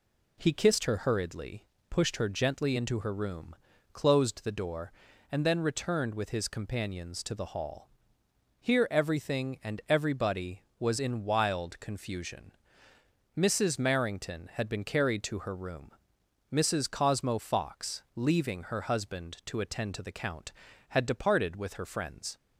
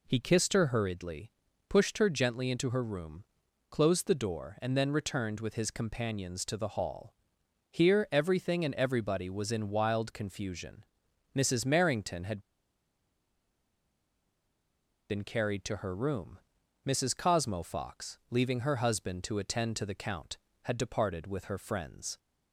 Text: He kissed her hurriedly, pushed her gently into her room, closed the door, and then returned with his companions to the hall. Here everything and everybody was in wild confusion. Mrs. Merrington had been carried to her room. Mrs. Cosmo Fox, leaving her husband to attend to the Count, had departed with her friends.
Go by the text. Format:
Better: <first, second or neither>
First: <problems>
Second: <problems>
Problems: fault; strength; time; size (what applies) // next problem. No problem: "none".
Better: first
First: none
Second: pauses between "had" and "been"; strong; at 12.3 s; 2.7 s long